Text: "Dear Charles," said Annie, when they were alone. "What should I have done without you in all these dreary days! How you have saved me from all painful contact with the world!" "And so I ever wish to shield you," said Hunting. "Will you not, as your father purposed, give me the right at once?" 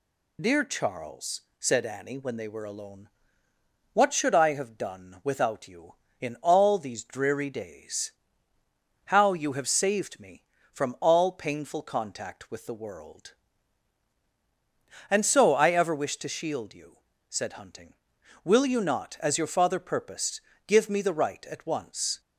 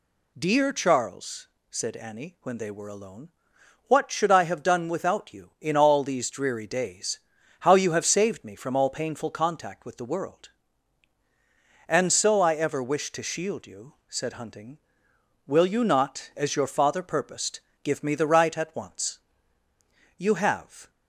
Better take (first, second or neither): first